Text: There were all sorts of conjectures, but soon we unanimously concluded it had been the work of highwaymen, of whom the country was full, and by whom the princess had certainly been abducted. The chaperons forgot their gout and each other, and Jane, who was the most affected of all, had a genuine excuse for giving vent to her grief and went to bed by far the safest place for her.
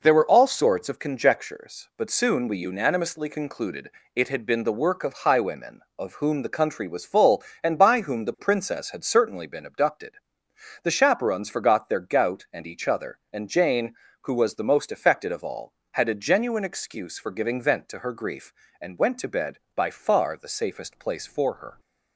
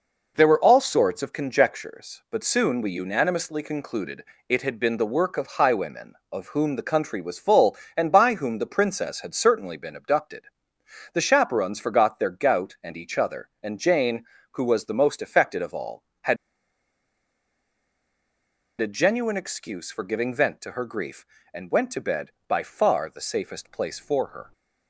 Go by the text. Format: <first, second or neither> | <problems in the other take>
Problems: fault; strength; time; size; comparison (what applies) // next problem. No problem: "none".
first | pauses between "concluded" and "it"; slight; at 4.2 s; 0.28 s long; slight in the first // pauses between "had" and "a"; strong; at 16.3 s; 2.4 s long